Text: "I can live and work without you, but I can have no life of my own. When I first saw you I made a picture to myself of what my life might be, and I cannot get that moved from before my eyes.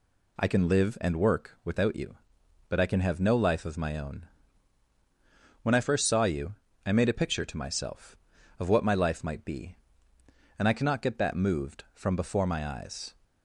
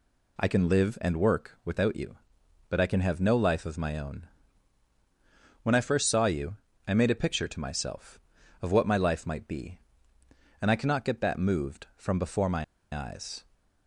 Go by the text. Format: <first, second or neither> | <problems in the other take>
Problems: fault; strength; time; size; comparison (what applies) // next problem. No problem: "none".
first | pauses between "you" and "I"; slight; at 6.5 s; 0.30 s long; slight in the first // pauses between "my" and "eyes"; slight; at 12.6 s; 0.29 s long